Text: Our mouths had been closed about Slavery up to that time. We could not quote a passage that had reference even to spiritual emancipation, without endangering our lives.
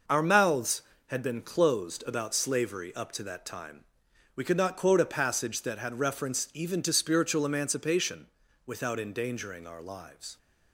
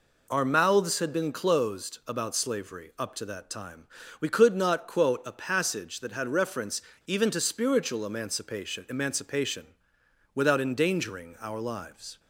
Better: first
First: none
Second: pauses between "reference" and "even"; slight; at 6.8 s; 0.23 s long // says "emancipation" twice; at 8.8 s

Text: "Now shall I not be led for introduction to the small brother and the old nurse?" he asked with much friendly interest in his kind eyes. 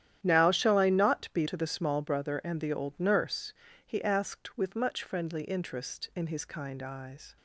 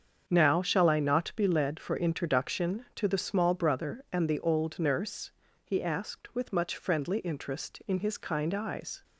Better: second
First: starts louder than the rest; strong; until 1.2 s; 11 dB // skips "led for introduction"; at 1.4 s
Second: starts louder than the rest; strong; until 1.2 s; 7.5 dB

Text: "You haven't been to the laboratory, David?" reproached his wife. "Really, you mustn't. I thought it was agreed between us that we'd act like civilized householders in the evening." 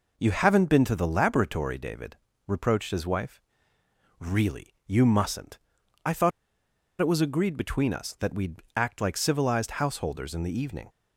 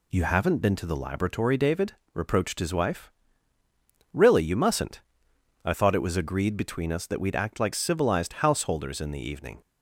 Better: second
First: pauses between "thought" and "it"; noticeable; at 6.3 s; 0.70 s long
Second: none

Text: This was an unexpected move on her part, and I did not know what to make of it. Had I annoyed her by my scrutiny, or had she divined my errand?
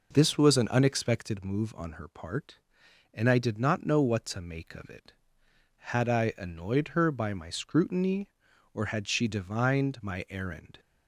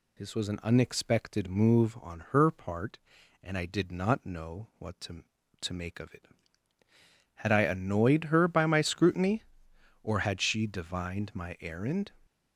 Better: first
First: none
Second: says "to" twice; at 5.5 s

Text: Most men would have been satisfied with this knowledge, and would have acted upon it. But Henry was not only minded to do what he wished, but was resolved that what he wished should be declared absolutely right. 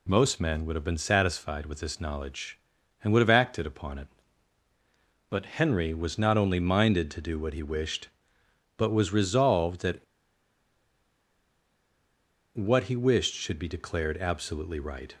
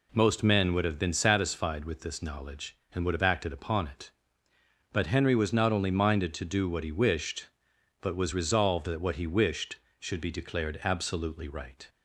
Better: second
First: pauses between "that" and "what"; strong; at 10.0 s; 2.5 s long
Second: none

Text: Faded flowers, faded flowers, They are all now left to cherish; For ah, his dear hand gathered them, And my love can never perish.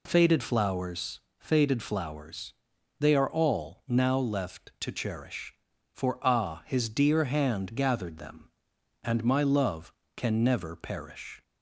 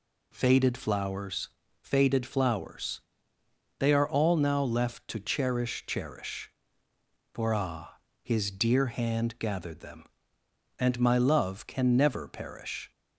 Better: first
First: none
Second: says "cherish" twice; at 5.8 s

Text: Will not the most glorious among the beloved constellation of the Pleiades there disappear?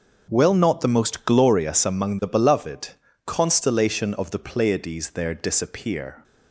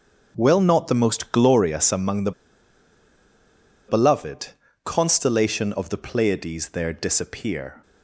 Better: first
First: starts louder than the rest; until 1.3 s; 6.5 dB // pauses between "beloved" and "constellation"; slight; at 2.9 s; 0.36 s long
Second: starts louder than the rest; until 1.3 s; 6.5 dB // pauses between "the" and "beloved"; strong; at 2.3 s; 1.5 s long // pauses between "beloved" and "constellation"; slight; at 4.4 s; 0.36 s long

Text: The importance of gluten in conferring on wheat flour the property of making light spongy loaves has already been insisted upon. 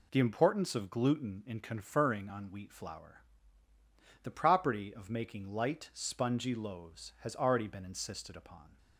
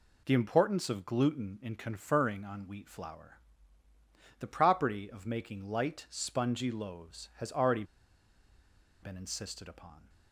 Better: first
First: pauses between "flour" and "the"; at 3.2 s; 1.0 s long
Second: pauses between "flour" and "the"; at 3.3 s; 1.0 s long // pauses between "already" and "been"; at 7.8 s; 1.1 s long

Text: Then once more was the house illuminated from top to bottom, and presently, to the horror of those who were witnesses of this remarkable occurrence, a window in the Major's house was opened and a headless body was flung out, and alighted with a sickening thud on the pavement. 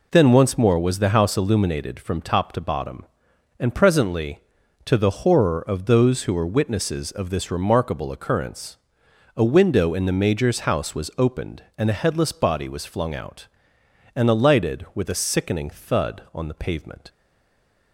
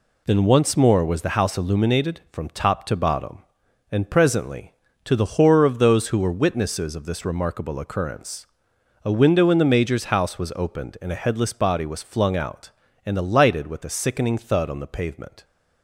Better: second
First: stays silent after the last word; slight; from 17.0 s on; 0.9 s long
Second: none

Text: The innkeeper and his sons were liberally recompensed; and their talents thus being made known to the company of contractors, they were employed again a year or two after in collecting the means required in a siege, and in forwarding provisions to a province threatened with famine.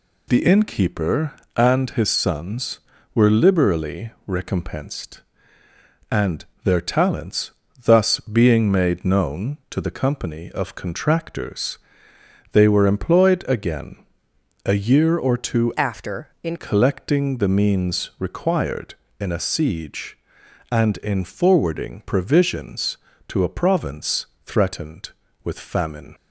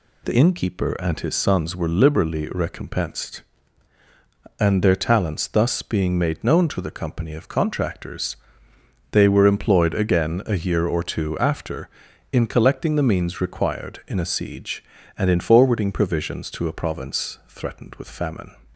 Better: second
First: pauses between "liberally" and "recompensed"; slight; at 4.1 s; 0.16 s long // pauses between "and" and "their"; slight; at 6.4 s; 0.20 s long // pauses between "talents" and "thus"; slight; at 7.4 s; 0.34 s long // pauses between "again" and "a"; noticeable; at 14.0 s; 0.62 s long // changes voice from "after" to "in"; from 15.7 to 16.5 s; 0.8 s long // pauses between "province" and "threatened"; slight; at 24.2 s; 0.20 s long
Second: none

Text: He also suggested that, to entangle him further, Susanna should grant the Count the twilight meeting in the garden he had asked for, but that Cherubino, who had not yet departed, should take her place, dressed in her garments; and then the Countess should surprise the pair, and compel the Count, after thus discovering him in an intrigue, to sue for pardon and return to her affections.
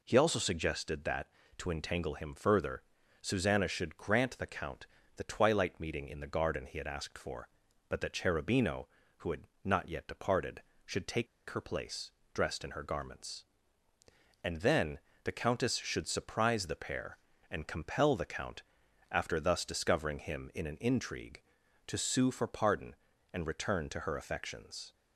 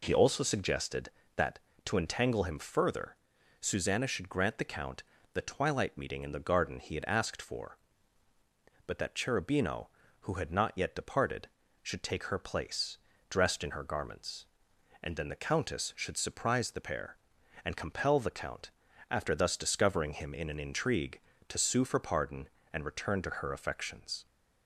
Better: second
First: pauses between "Count" and "the"; slight; at 4.8 s; 0.32 s long // pauses between "had" and "not"; slight; at 9.4 s; 0.16 s long // pauses between "take" and "her"; slight; at 11.2 s; 0.23 s long // pauses between "then" and "the"; slight; at 15.0 s; 0.24 s long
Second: pauses between "Count" and "the"; slight; at 5.0 s; 0.30 s long

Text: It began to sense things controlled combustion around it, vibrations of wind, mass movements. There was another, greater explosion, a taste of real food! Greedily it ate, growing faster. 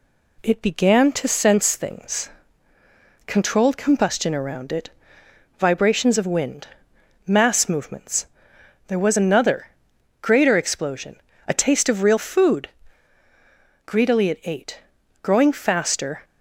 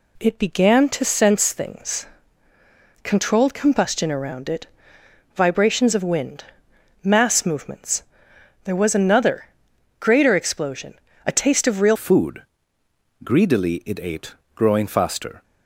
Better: first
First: pauses between "things" and "controlled"; noticeable; at 2.2 s; 0.96 s long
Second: pauses between "things" and "controlled"; noticeable; at 2.0 s; 0.96 s long // changes voice at "food"; from 11.9 s on; 3.5 s long

